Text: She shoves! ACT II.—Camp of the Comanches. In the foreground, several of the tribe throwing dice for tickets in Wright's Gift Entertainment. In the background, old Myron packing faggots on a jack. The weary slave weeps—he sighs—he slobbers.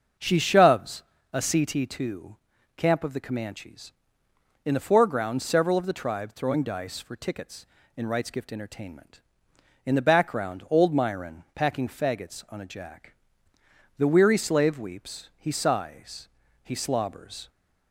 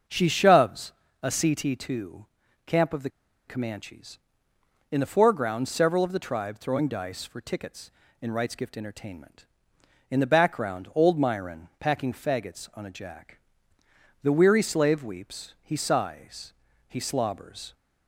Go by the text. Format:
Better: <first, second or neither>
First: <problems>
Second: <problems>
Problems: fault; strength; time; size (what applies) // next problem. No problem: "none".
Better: first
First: starts louder than the rest; until 1.4 s; 6.5 dB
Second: starts louder than the rest; until 1.3 s; 6.5 dB // pauses between "the" and "Comanches"; at 3.0 s; 0.38 s long